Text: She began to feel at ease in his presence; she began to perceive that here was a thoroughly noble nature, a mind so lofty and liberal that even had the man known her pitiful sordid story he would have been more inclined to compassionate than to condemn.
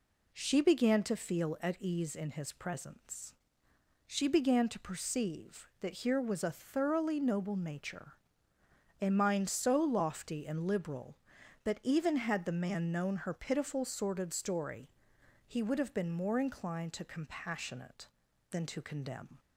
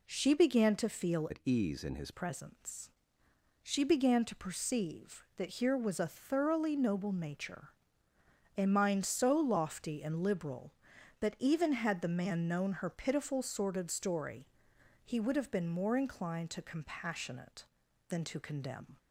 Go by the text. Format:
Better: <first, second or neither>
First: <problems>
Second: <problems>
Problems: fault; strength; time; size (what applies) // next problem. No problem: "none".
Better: first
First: pauses between "story" and "he"; noticeable; at 14.8 s; 0.60 s long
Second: changes voice from "at" to "his"; from 1.3 to 2.1 s; 0.8 s long // pauses between "story" and "he"; noticeable; at 14.4 s; 0.60 s long